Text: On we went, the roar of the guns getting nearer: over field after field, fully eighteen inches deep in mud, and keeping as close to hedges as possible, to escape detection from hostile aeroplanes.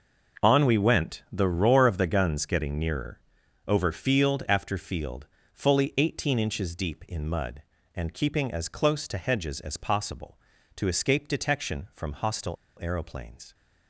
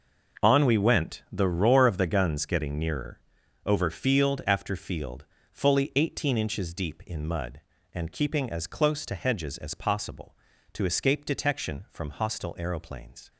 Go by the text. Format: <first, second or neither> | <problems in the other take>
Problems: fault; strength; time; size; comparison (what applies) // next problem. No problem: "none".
second | pauses between "hostile" and "aeroplanes"; slight; at 12.5 s; 0.25 s long